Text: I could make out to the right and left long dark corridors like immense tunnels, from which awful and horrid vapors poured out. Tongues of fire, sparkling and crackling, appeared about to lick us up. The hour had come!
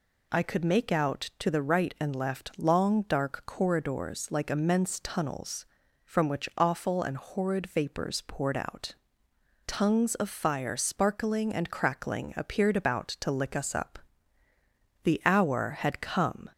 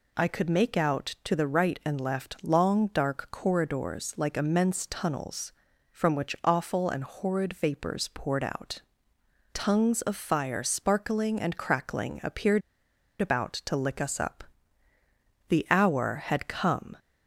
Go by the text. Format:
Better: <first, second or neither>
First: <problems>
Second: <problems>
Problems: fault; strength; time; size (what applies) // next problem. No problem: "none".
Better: first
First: none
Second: pauses between "appeared" and "about"; noticeable; at 12.6 s; 0.59 s long